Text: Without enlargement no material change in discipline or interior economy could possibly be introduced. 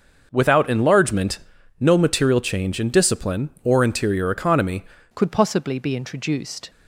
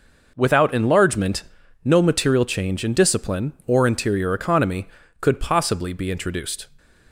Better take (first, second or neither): second